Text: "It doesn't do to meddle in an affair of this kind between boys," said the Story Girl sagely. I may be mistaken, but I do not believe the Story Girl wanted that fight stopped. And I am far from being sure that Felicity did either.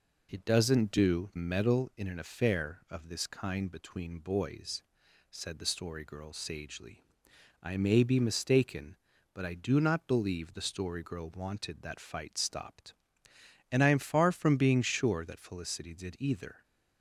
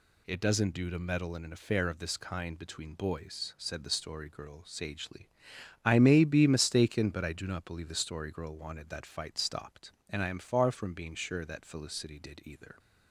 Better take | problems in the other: second | skips "to"; at 1.3 s

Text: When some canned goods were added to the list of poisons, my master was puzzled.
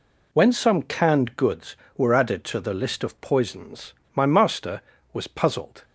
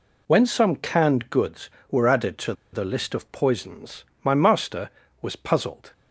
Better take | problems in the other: first | pauses between "to" and "the"; slight; at 2.5 s; 0.19 s long

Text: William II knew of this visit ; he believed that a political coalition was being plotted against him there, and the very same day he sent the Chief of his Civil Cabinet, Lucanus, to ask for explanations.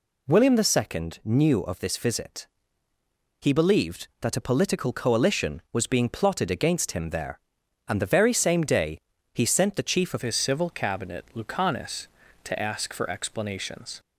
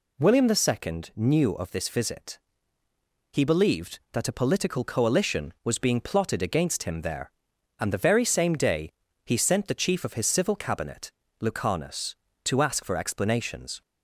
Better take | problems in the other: second | pauses between "day" and "he"; at 8.9 s; 0.38 s long; also in the second // changes voice at "his"; from 10.2 s on; 3.7 s long

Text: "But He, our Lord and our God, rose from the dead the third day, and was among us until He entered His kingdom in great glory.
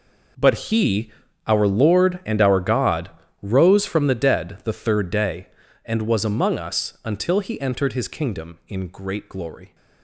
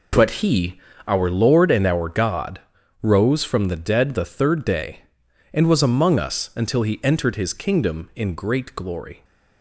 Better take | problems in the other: second | gets quieter; strong; throughout; 14.5 dB

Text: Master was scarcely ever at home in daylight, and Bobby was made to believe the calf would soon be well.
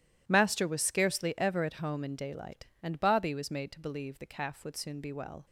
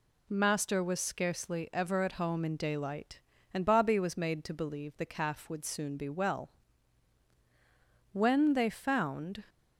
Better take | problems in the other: first | goes on to say "When they found"; noticeable; from 8.1 s on; 1.3 s long

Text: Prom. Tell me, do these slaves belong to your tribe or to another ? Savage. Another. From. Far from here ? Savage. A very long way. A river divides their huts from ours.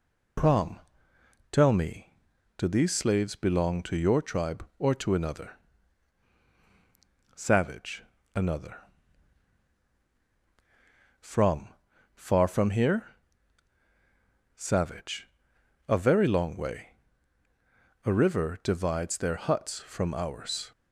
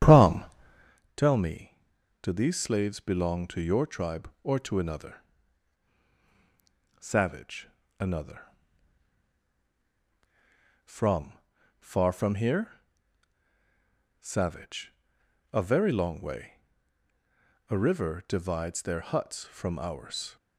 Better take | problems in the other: first | starts louder than the rest; strong; until 1.0 s; 9.5 dB

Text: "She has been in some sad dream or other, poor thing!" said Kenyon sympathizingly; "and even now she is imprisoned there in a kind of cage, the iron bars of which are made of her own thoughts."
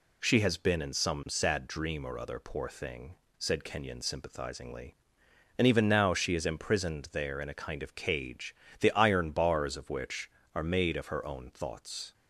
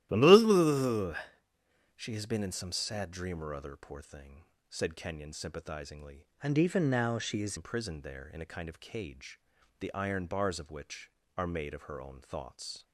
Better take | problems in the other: first | changes voice from "and" to "is"; from 6.4 to 7.5 s; 1.1 s long

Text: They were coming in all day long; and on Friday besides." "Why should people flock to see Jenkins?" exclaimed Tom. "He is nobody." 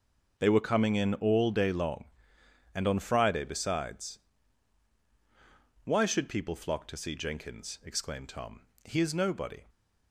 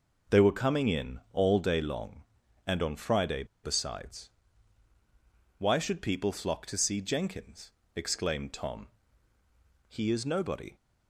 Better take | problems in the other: first | pauses between "Friday" and "besides"; slight; at 3.4 s; 0.20 s long

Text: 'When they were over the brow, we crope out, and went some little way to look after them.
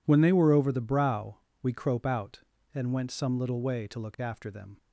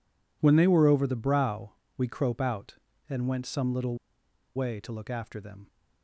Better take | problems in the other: first | pauses between "little" and "way"; noticeable; at 3.9 s; 0.58 s long

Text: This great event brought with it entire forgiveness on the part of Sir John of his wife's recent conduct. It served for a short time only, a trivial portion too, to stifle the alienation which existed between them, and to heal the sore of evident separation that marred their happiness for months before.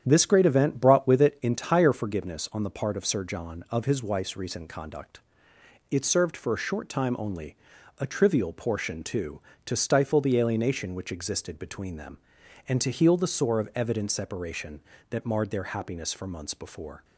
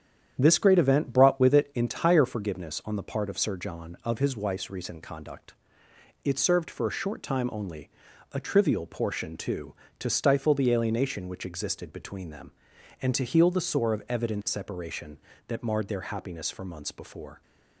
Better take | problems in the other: neither | starts louder than the rest; strong; the same in both

